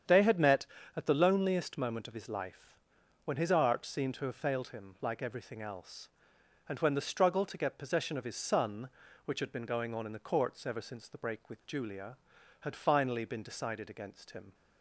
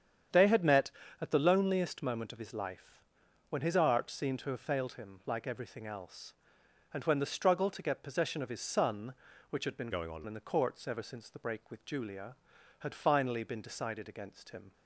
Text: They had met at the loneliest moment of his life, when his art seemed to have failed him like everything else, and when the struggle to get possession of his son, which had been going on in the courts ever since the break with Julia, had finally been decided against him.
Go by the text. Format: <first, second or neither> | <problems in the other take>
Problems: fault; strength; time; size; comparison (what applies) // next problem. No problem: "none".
first | starts louder than the rest; strong; until 1.6 s; 8.5 dB; strong in the first // changes voice from "going" to "on"; from 9.9 to 10.2 s; 0.3 s long